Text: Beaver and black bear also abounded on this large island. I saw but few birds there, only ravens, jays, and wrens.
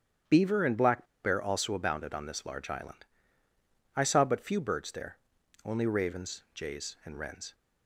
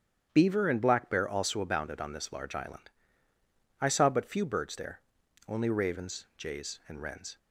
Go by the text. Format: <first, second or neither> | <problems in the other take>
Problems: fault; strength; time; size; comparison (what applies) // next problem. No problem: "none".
second | starts louder than the rest; strong; until 1.4 s; 9 dB; strong in the second // pauses between "black" and "bear"; slight; at 1.0 s; 0.18 s long